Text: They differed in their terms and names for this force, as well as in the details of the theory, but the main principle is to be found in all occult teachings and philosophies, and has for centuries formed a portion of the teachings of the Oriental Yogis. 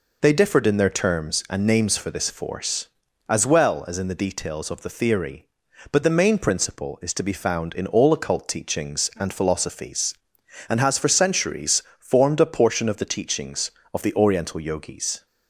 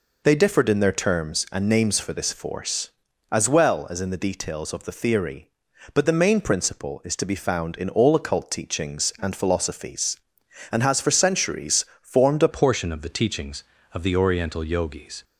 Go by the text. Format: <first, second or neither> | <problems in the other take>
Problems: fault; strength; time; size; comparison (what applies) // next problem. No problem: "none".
first | pauses between "centuries" and "formed"; slight; at 11.8 s; 0.16 s long; slight in the first // changes voice at "portion"; from 12.4 s on; 2.8 s long